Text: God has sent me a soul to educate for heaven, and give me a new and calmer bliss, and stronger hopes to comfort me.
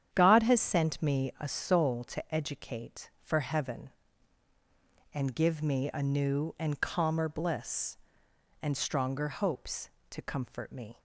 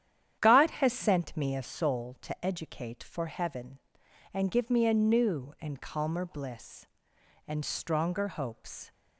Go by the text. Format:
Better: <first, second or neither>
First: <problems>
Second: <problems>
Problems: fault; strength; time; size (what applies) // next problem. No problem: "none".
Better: first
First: starts louder than the rest; strong; until 1.1 s; 9 dB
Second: starts louder than the rest; strong; until 1.4 s; 10 dB // stops before "to comfort me"; at 8.9 s